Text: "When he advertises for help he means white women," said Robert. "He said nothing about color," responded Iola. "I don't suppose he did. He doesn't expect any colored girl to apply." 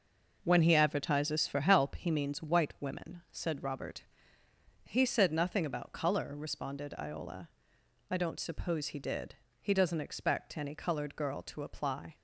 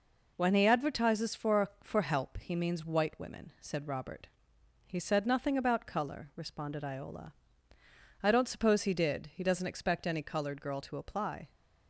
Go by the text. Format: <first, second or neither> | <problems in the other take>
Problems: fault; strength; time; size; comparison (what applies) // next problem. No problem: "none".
first | says "for" twice; at 1.8 s